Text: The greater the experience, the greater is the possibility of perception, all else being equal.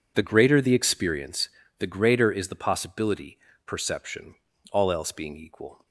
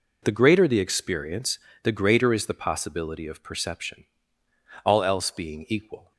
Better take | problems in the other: second | skips "of"; at 3.5 s

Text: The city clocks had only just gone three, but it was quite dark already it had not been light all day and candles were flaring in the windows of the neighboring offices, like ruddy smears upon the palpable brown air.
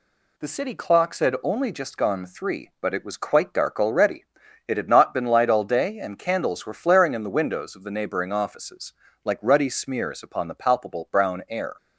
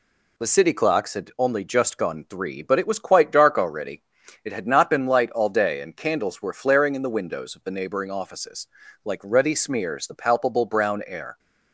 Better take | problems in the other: first | pauses between "already" and "it"; at 4.0 s; 0.40 s long; also in the first // skips "upon"; at 10.0 s

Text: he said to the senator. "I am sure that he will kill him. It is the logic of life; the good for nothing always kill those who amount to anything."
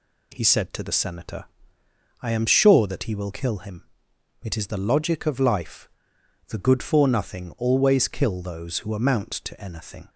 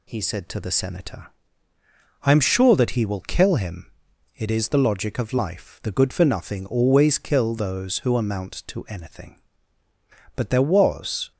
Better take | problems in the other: first | goes on to say "But there was"; noticeable; from 10.3 s on; 0.94 s long

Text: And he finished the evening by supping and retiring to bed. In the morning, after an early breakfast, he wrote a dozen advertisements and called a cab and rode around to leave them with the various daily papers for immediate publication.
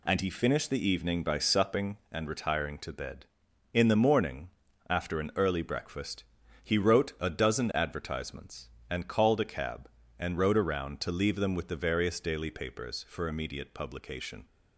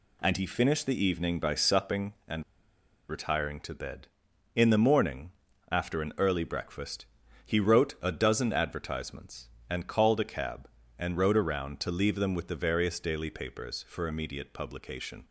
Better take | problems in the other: first | pauses between "and" and "retiring"; noticeable; at 2.4 s; 0.65 s long

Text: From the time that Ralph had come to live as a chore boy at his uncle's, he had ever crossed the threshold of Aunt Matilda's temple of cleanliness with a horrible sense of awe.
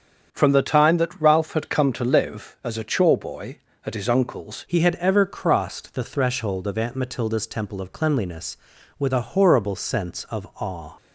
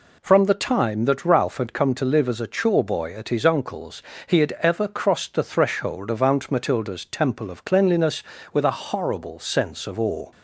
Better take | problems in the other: second | starts louder than the rest; strong; until 1.3 s; 7.5 dB // changes voice at "he"; from 4.6 s on; 6.3 s long

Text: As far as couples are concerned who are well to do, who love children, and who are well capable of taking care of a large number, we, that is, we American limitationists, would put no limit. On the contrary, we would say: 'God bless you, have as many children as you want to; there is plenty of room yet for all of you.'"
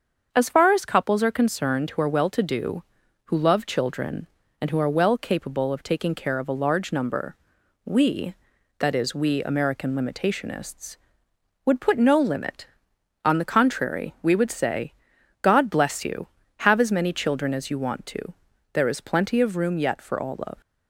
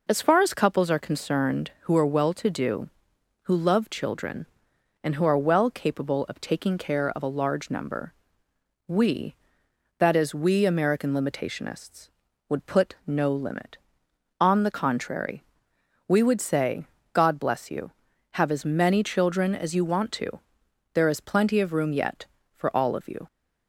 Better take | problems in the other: second | starts louder than the rest; until 1.3 s; 7 dB // stops before "you"; at 20.6 s

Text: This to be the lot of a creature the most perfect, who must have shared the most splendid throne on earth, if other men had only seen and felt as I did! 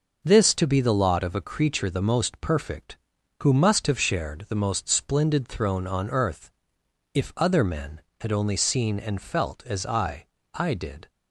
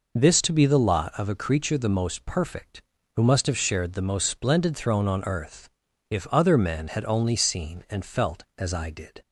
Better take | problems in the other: second | says "I" twice; at 10.5 s

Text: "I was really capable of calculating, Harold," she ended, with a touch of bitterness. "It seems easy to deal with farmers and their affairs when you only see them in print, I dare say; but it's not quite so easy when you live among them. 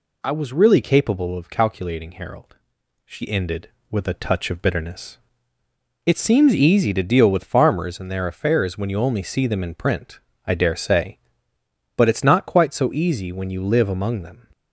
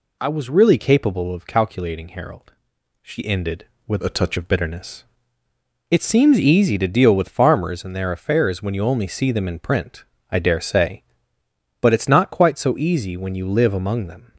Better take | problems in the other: first | changes voice from "a" to "touch"; from 4.0 to 4.3 s; 0.3 s long

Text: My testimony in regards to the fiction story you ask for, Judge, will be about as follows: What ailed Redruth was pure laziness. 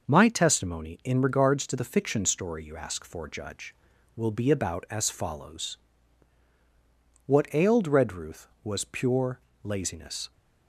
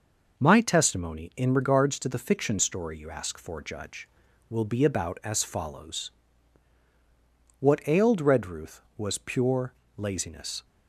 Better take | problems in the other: neither | pauses between "pure" and "laziness"; slight; the same in both

